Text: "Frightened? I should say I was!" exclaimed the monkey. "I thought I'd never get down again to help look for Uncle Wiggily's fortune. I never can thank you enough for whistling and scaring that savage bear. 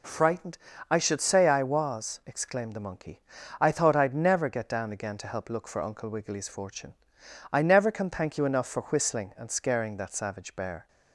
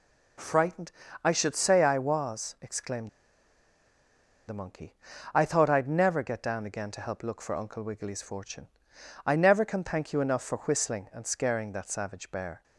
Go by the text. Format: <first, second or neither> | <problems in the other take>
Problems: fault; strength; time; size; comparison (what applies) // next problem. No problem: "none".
first | pauses between "exclaimed" and "the"; strong; at 3.0 s; 1.3 s long